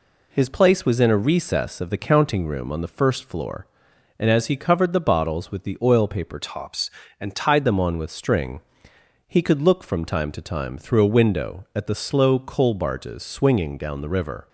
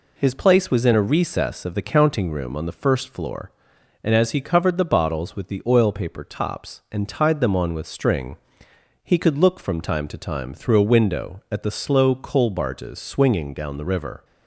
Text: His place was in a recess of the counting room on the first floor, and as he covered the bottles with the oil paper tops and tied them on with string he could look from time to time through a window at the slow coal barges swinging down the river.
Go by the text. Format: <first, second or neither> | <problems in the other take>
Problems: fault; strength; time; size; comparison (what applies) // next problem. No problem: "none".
second | changes voice from "tops" to "tied"; from 6.4 to 7.6 s; 1.2 s long // pauses between "string" and "he"; noticeable; at 8.6 s; 0.70 s long; noticeable in the second